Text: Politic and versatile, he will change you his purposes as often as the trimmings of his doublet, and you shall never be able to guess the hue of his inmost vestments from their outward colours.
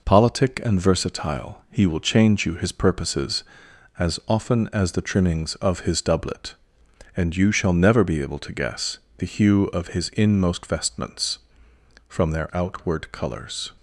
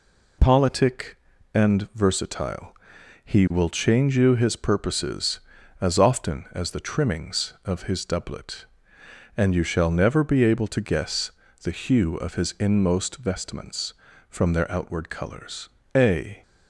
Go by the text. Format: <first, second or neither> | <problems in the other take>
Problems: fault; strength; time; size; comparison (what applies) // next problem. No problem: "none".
first | pauses between "guess" and "the"; slight; at 11.2 s; 0.32 s long; slight in the first // goes on to say "A"; slight; from 15.9 s on; 0.48 s long